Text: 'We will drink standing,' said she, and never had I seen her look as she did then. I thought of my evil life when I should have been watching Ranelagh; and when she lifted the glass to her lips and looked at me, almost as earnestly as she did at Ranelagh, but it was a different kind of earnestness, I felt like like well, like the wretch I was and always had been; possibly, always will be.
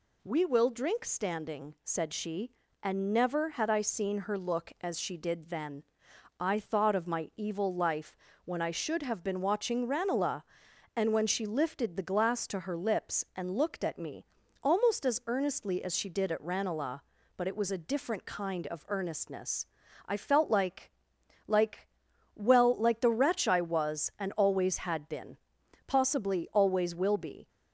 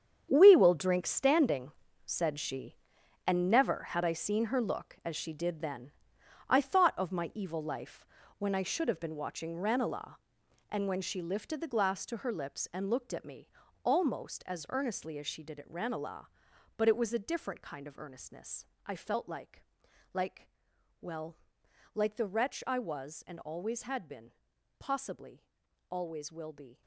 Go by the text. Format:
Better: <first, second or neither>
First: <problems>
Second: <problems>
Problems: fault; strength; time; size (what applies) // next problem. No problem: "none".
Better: first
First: pauses between "life" and "when"; slight; at 8.1 s; 0.28 s long // pauses between "like" and "like"; noticeable; at 20.8 s; 0.58 s long // pauses between "like" and "well"; noticeable; at 21.8 s; 0.48 s long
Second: gets quieter; strong; throughout; 13 dB // pauses between "life" and "when"; slight; at 8.0 s; 0.32 s long // pauses between "like" and "like"; noticeable; at 19.6 s; 0.50 s long // pauses between "like" and "well"; noticeable; at 20.4 s; 0.54 s long